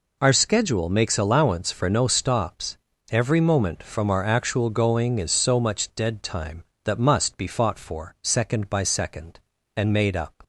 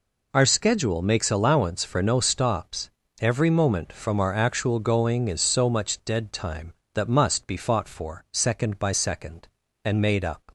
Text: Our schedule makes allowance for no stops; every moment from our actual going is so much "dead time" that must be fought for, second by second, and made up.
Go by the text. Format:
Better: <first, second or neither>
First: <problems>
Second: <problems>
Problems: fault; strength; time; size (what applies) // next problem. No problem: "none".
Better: neither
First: none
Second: none